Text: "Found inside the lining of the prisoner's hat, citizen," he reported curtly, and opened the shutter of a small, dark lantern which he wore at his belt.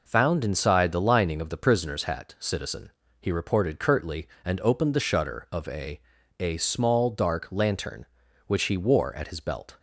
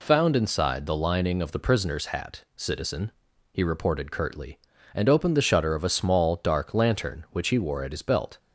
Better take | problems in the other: second | says "a" twice; at 6.3 s

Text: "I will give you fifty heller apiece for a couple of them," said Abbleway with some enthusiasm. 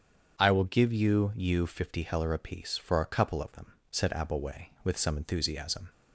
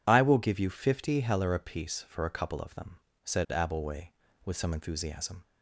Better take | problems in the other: second | starts louder than the rest; strong; until 1.4 s; 7.5 dB // says "you" twice; at 1.3 s

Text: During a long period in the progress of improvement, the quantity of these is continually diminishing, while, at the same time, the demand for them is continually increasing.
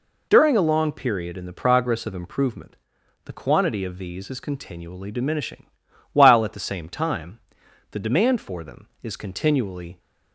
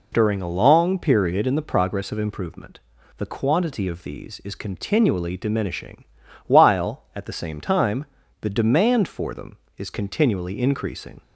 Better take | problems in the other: second | stops before "increasing"; at 9.9 s

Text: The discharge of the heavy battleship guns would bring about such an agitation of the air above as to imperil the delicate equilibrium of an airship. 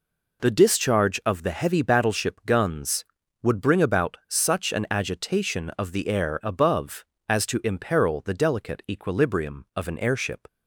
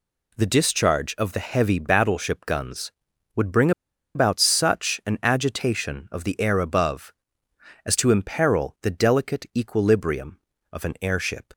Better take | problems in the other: first | pauses between "bring" and "about"; at 3.7 s; 0.44 s long

